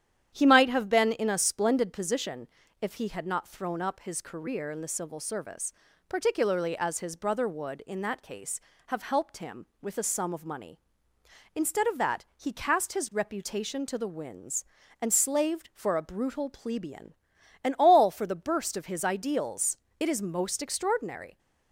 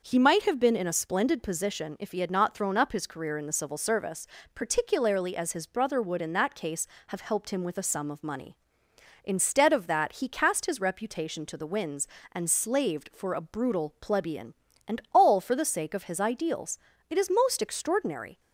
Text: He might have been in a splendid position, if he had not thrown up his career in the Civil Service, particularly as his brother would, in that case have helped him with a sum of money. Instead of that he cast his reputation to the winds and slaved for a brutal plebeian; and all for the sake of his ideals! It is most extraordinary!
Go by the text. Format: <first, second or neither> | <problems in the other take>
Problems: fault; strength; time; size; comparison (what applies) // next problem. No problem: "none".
second | starts louder than the rest; strong; until 1.3 s; 10 dB; noticeable in the second // says "burst" for "sake"; at 18.3 s